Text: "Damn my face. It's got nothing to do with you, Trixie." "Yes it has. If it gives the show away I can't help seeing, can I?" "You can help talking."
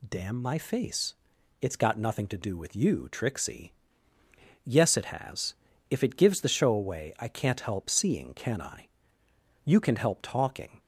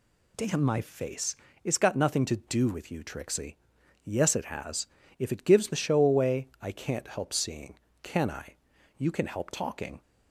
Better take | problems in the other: neither | none

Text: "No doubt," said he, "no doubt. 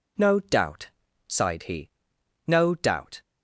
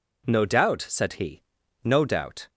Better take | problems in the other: second | says "sighed" for "said"; at 1.2 s

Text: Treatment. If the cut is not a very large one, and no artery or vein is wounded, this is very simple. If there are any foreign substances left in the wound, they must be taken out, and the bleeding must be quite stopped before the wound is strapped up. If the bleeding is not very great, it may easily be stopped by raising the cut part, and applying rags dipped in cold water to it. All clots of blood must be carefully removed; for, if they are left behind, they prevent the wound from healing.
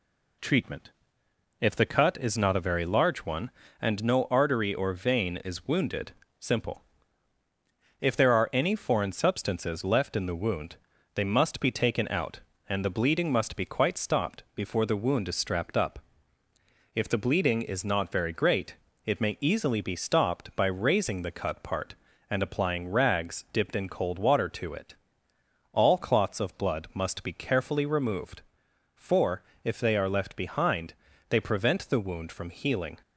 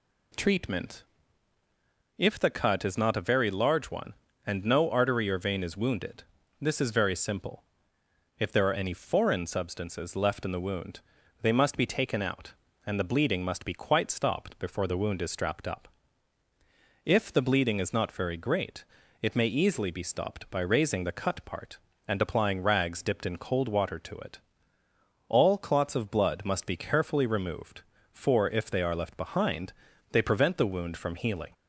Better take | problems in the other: second | skips "this is very"; at 6.2 s

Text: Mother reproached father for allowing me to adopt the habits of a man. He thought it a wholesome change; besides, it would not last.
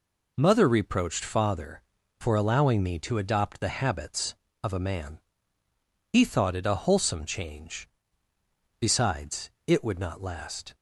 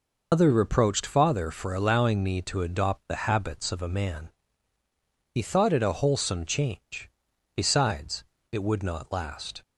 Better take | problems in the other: first | loses the start of "Mother"; at 0.3 s; 125 ms

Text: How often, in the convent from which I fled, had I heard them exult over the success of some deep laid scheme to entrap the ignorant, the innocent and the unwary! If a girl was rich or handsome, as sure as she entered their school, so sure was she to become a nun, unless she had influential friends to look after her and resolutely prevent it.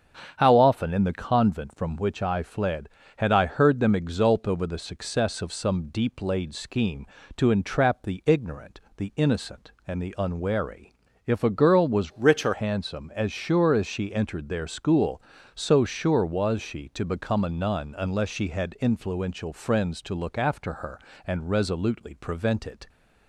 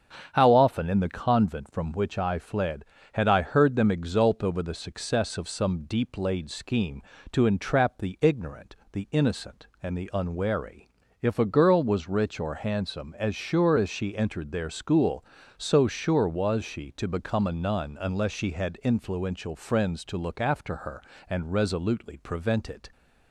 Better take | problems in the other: second | starts louder than the rest; strong; until 1.3 s; 8 dB; strong in the second // changes voice from "rich" to "or"; from 12.1 to 12.5 s; 0.4 s long

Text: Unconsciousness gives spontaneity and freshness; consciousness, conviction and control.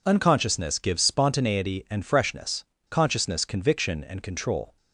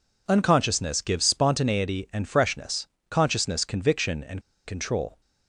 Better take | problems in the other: first | pauses between "and" and "control"; slight; at 4.4 s; 0.24 s long

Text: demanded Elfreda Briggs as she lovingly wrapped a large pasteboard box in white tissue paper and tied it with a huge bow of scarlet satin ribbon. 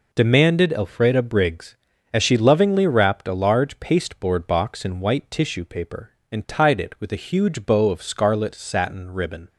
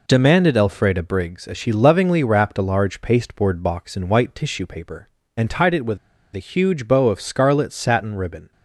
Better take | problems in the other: first | pauses between "with" and "a"; at 5.9 s; 0.37 s long

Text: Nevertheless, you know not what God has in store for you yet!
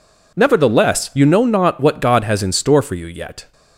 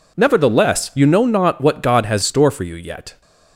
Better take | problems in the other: first | skips "in"; at 2.2 s

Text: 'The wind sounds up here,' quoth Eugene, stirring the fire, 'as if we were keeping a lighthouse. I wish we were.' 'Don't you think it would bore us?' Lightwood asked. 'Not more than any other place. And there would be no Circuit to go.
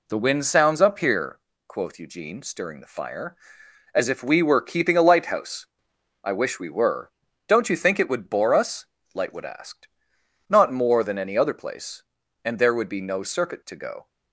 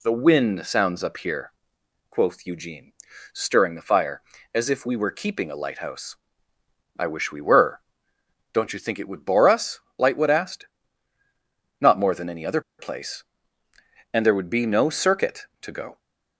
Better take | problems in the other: first | pauses between "other" and "place"; slight; at 12.6 s; 0.18 s long

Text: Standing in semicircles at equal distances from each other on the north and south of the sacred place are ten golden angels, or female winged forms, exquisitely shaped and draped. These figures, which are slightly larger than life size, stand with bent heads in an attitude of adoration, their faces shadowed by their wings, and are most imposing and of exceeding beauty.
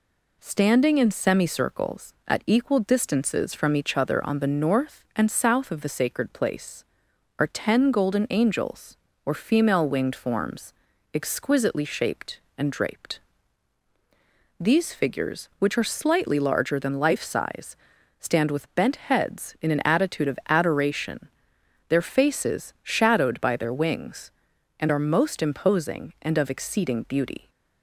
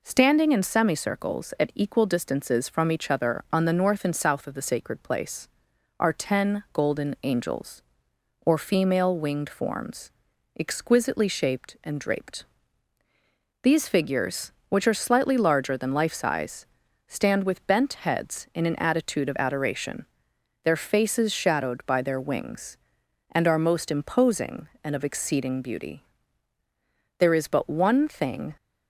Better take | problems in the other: first | goes on to say "There is but one thing"; from 27.1 s on; 1.3 s long

